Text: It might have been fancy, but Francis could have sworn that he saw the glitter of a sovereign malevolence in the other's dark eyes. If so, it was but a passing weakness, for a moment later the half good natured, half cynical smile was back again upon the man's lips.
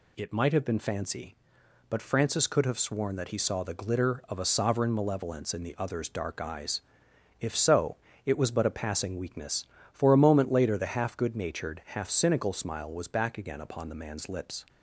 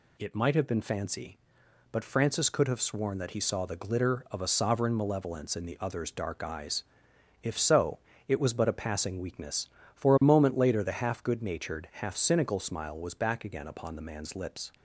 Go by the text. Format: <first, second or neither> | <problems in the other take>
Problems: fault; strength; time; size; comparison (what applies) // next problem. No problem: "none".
neither | none